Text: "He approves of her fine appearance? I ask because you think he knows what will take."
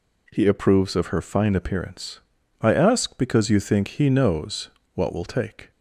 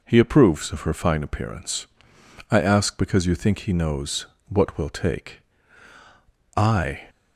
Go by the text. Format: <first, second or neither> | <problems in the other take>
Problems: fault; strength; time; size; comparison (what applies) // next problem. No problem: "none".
first | pauses between "knows" and "what"; slight; at 4.2 s; 0.24 s long; slight in the first // goes on to say "I"; slight; from 6.5 s on; 0.46 s long